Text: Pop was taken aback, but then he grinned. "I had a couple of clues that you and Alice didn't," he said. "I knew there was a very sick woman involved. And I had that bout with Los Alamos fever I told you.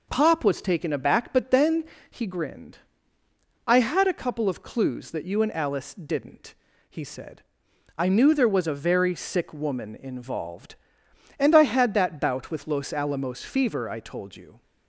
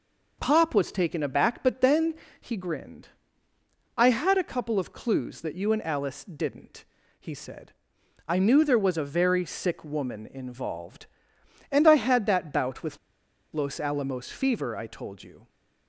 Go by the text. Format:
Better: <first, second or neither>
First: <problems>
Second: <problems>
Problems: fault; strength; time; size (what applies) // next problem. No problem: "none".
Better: first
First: pauses between "then" and "he"; slight; at 1.8 s; 0.26 s long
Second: pauses between "then" and "he"; slight; at 2.1 s; 0.26 s long // pauses between "with" and "Los"; noticeable; at 12.9 s; 0.56 s long